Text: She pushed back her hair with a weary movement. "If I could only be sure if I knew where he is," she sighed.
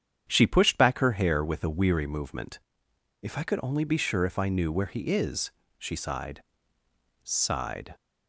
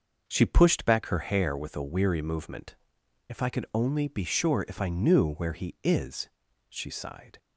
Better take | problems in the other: second | starts louder than the rest; strong; until 1.2 s; 8.5 dB // says "sighed" twice; at 7.2 s

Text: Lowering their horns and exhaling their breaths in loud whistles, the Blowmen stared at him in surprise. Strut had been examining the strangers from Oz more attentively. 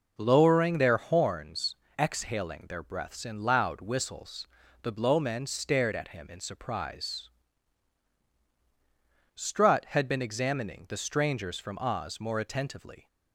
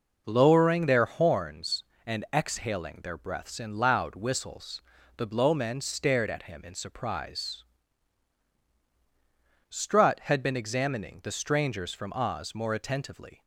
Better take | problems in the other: second | skips "and"; at 1.8 s

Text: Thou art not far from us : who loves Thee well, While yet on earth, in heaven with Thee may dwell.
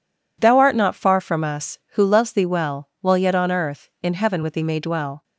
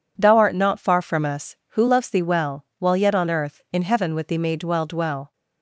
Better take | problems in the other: first | says "dwell" twice; at 4.8 s

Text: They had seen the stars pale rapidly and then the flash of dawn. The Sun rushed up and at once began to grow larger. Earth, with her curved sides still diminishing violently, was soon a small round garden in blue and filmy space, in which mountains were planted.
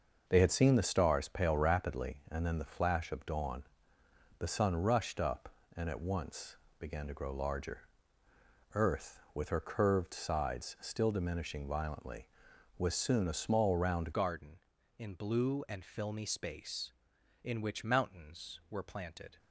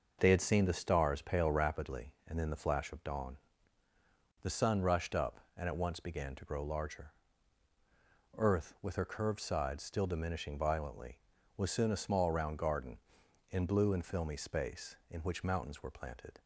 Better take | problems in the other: second | starts louder than the rest; noticeable; until 1.2 s; 6 dB // pauses between "once" and "began"; slight; at 6.5 s; 0.22 s long // changes voice at "garden"; from 14.1 s on; 5.2 s long

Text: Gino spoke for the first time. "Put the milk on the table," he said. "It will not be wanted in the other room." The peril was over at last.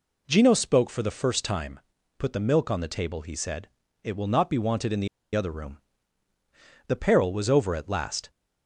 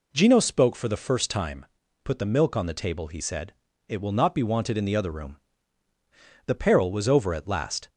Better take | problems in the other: second | pauses between "the" and "other"; slight; at 5.0 s; 0.27 s long

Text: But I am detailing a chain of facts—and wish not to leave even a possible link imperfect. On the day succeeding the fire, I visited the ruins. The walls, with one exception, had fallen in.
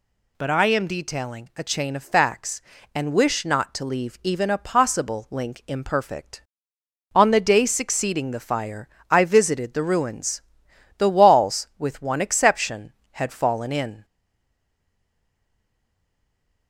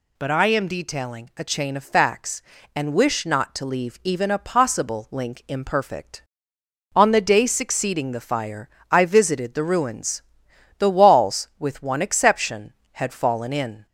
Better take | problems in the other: second | stays silent after the last word; strong; from 14.0 s on; 2.6 s long

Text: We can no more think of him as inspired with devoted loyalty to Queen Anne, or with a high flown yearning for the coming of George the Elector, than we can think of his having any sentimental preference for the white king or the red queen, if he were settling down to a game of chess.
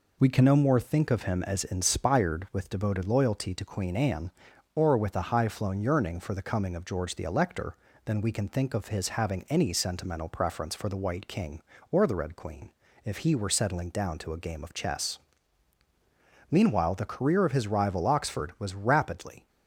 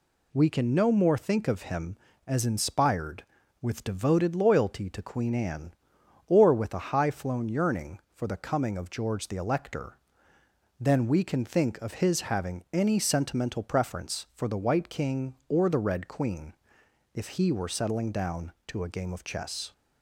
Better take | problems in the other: second | goes on to say "Meanwhile the career of his rival Oxford was rapidly"; strong; from 16.4 s on; 2.9 s long

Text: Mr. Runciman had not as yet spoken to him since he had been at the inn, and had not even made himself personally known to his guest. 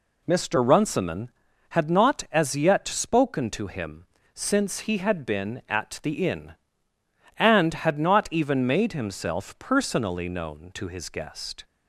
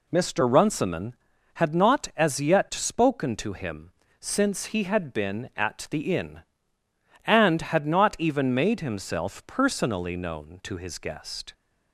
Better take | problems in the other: neither | pauses between "him" and "since"; slight; the same in both

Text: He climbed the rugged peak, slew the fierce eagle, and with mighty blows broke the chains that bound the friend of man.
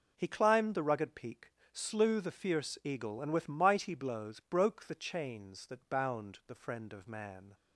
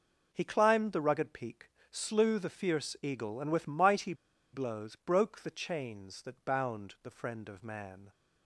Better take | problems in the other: first | pauses between "mighty" and "blows"; at 4.1 s; 0.39 s long

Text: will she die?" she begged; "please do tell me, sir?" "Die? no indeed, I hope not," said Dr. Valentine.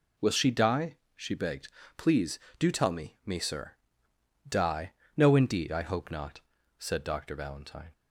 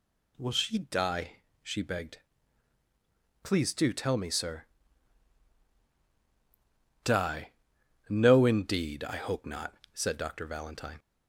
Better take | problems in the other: second | says "me" twice; at 3.2 s

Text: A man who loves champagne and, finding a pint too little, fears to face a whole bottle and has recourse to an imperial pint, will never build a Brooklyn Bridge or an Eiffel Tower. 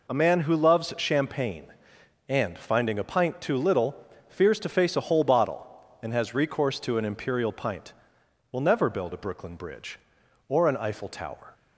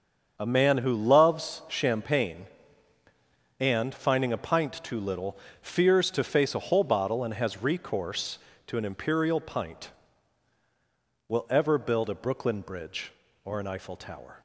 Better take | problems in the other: first | starts louder than the rest; until 1.3 s; 6.5 dB // says "ever" for "never"; at 11.4 s

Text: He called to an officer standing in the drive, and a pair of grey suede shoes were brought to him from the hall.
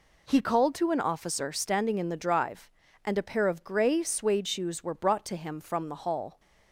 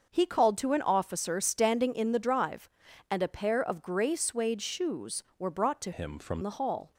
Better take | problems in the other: first | starts louder than the rest; until 1.1 s; 6 dB // changes voice from "him" to "from"; from 5.9 to 6.3 s; 0.4 s long

